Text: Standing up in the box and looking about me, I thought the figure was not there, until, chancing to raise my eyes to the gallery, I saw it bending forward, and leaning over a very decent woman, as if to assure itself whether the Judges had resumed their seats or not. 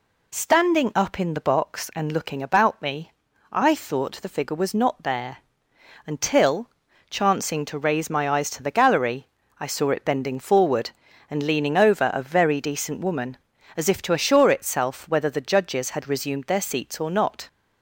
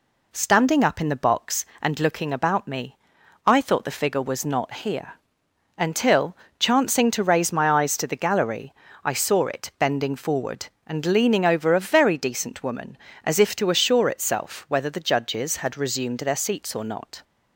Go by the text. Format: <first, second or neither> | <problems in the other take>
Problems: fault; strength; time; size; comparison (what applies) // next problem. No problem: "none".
first | says "here" for "there"; at 4.7 s